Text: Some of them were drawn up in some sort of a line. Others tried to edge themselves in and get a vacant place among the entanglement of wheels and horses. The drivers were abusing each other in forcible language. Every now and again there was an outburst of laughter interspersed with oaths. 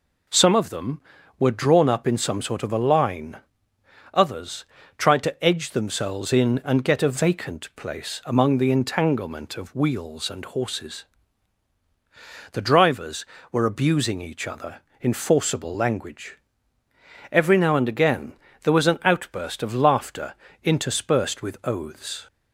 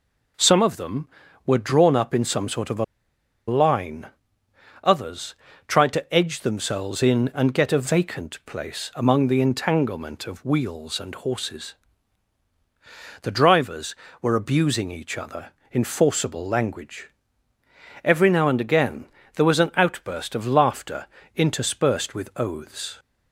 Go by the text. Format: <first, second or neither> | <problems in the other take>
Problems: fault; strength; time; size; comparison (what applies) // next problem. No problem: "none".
first | pauses between "a" and "line"; noticeable; at 2.8 s; 0.63 s long // pauses between "Others" and "tried"; slight; at 5.3 s; 0.32 s long; slight in the first // pauses between "again" and "there"; slight; at 19.0 s; 0.30 s long; slight in the first // pauses between "laughter" and "interspersed"; slight; at 21.0 s; 0.28 s long; slight in the first